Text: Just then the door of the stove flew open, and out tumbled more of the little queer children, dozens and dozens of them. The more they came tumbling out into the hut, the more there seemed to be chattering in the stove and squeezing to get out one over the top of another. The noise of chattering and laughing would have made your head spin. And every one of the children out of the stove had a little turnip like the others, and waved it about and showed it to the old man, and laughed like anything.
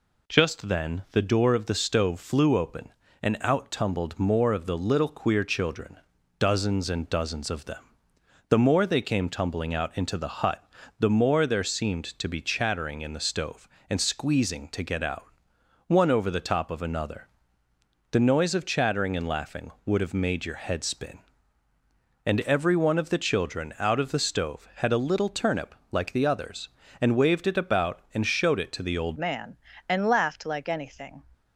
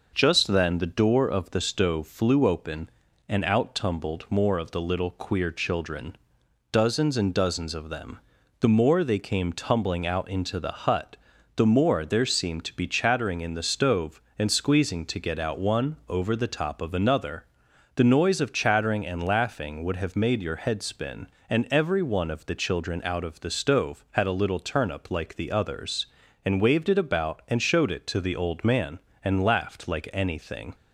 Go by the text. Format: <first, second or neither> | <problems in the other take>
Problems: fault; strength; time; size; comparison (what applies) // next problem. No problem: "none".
second | pauses between "out" and "one"; noticeable; at 15.2 s; 0.62 s long // pauses between "turnip" and "like"; slight; at 25.7 s; 0.16 s long // changes voice at "man"; from 29.1 s on; 2.1 s long